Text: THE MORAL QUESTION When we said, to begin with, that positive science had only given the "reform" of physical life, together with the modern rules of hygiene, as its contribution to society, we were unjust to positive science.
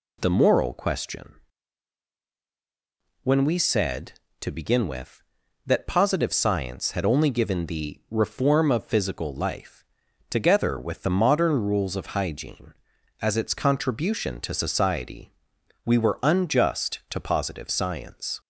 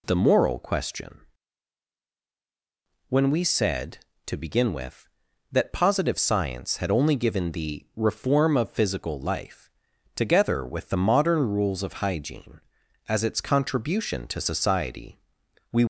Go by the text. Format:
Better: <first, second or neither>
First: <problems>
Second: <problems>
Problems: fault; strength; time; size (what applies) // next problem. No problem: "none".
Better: first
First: pauses between "QUESTION" and "When"; strong; at 1.3 s; 1.8 s long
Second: pauses between "QUESTION" and "When"; strong; at 1.2 s; 1.8 s long // stops before "were unjust to positive science"; at 15.8 s